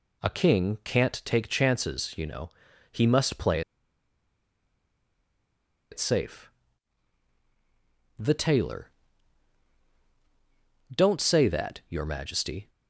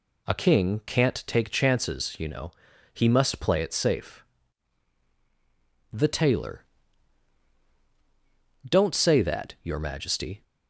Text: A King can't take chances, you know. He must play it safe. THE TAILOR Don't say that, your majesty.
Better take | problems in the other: second | pauses between "play" and "it"; strong; at 3.6 s; 2.3 s long // pauses between "TAILOR" and "Don't"; strong; at 8.8 s; 2.0 s long; strong in the second

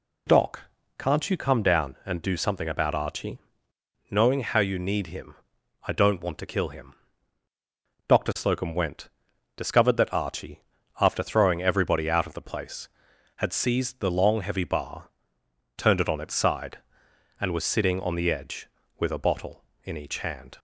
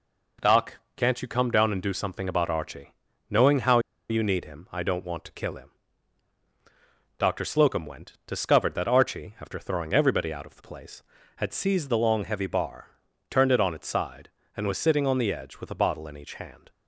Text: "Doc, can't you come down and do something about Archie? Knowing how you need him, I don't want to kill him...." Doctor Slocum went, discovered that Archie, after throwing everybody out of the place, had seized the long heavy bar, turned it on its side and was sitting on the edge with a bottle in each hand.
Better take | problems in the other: first | pauses between "how" and "you"; slight; at 3.7 s; 0.30 s long

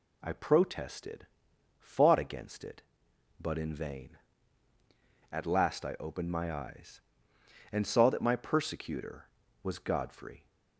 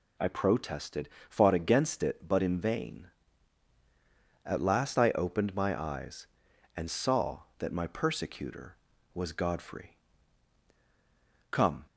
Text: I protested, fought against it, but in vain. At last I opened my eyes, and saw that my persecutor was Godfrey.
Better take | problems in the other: first | goes on to say "Come"; slight; from 11.4 s on; 0.34 s long

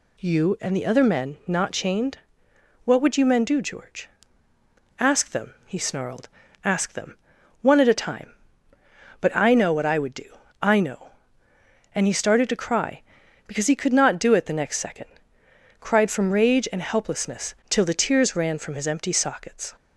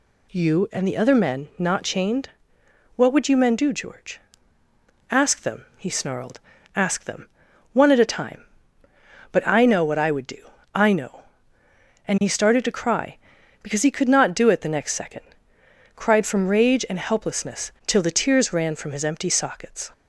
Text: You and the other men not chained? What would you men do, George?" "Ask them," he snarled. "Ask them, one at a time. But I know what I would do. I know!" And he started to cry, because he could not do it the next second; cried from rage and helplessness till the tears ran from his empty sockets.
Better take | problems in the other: neither | none

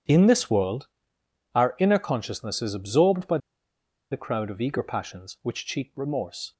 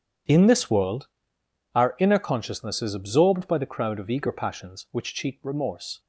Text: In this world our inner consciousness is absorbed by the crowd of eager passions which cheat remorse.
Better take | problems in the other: second | pauses between "world" and "our"; noticeable; at 0.8 s; 0.70 s long; noticeable in the second // pauses between "by" and "the"; noticeable; at 3.3 s; 0.73 s long

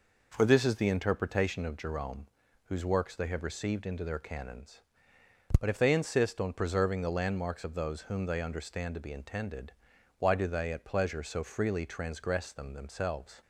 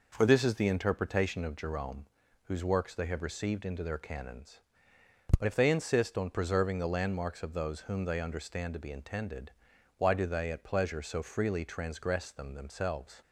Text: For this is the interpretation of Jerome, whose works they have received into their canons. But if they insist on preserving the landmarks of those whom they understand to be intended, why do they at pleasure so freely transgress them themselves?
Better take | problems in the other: neither | none

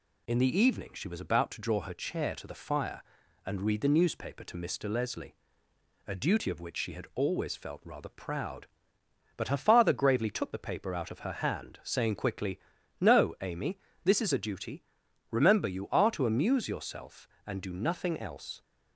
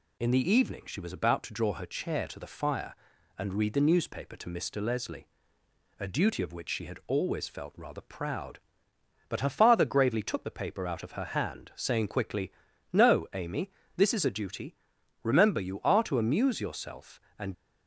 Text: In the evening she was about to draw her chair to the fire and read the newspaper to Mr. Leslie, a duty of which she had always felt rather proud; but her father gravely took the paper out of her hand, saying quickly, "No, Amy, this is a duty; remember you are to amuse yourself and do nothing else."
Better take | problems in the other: first | stops before "do nothing else"; at 17.5 s

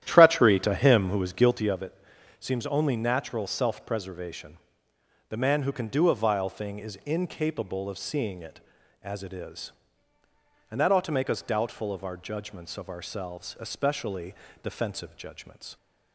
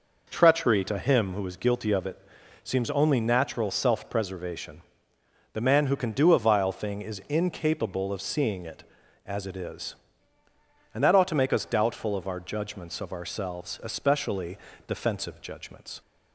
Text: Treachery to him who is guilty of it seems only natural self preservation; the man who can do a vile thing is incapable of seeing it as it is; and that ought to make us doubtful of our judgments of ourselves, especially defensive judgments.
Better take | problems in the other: second | starts louder than the rest; strong; until 1.7 s; 11.5 dB // pauses between "it" and "seems"; at 1.9 s; 0.44 s long; also in the second // pauses between "especially" and "defensive"; slight; at 14.3 s; 0.28 s long; slight in the second

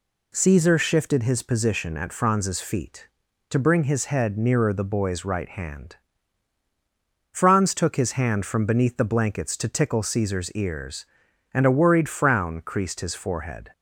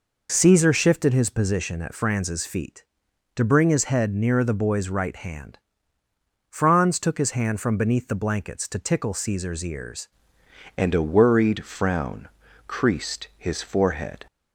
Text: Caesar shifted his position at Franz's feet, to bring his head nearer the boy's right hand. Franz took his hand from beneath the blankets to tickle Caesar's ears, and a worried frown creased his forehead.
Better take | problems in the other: first | changes voice at "and"; from 10.7 s on; 3.5 s long // pauses between "frown" and "creased"; at 12.2 s; 0.40 s long

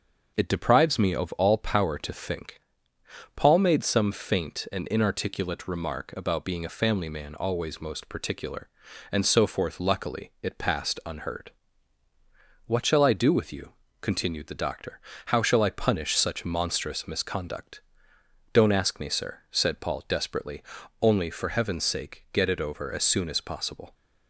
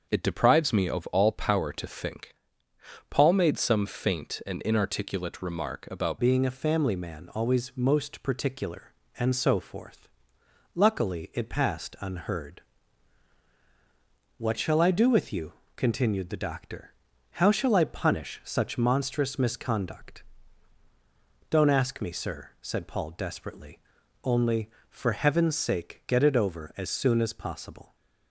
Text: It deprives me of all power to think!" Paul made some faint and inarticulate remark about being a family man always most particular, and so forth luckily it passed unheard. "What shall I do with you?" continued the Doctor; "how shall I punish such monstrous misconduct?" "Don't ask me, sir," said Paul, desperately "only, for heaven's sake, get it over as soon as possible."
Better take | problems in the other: first | starts louder than the rest; until 1.1 s; 6.5 dB; also in the first // changes voice at "being"; from 6.1 s on; 21.8 s long // pauses between "forth" and "luckily"; noticeable; at 10.0 s; 0.66 s long // pauses between "desperately" and "only"; at 23.7 s; 0.44 s long; also in the first

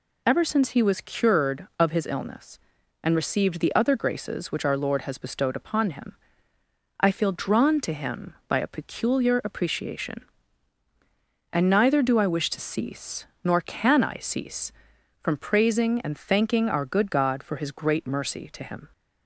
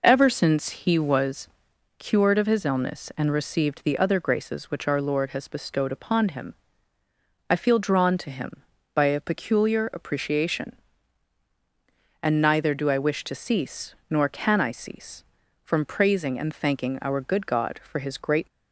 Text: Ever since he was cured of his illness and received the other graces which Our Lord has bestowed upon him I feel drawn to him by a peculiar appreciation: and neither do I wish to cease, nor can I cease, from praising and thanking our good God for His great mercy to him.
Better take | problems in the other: first | pauses between "was" and "cured"; noticeable; at 1.4 s; 0.48 s long // pauses between "him" and "I"; noticeable; at 6.5 s; 0.96 s long; noticeable in the first // stops before "mercy to him"; at 18.4 s

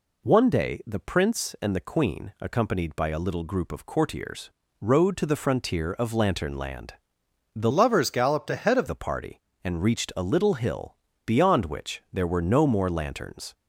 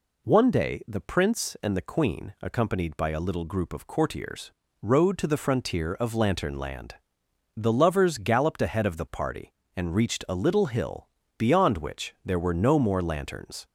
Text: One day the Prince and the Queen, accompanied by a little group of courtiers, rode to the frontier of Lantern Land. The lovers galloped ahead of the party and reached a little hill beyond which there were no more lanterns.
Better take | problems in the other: second | changes voice from "lovers" to "of"; from 7.7 to 8.8 s; 1.1 s long // pauses between "hill" and "beyond"; slight; at 10.9 s; 0.32 s long; slight in the second

